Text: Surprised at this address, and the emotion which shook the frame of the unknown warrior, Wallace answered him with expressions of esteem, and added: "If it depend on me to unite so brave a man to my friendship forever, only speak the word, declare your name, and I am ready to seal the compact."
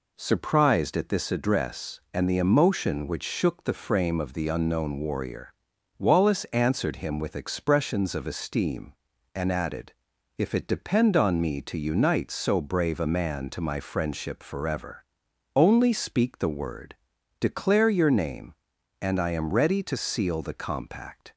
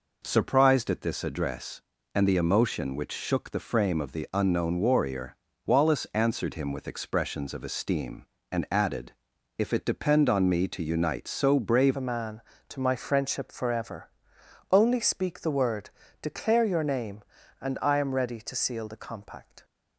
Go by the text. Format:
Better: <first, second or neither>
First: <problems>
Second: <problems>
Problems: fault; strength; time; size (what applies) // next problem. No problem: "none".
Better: first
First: none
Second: changes voice at "a"; from 11.9 s on; 7.7 s long